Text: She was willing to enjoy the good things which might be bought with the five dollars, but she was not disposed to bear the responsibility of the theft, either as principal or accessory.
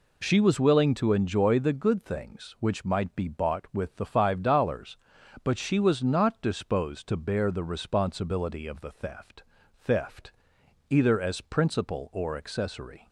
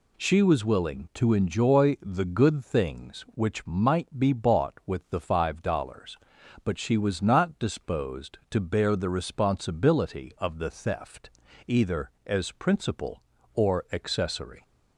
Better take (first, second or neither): second